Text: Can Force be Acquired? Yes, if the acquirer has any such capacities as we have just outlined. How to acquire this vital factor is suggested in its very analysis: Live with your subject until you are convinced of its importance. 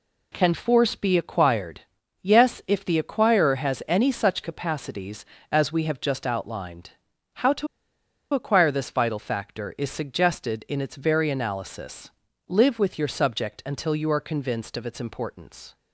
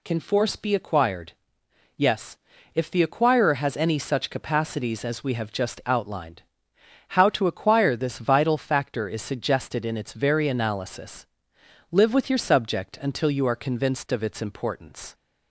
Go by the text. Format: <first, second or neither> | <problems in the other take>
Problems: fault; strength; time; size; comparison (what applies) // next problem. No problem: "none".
second | pauses between "to" and "acquire"; noticeable; at 7.6 s; 0.66 s long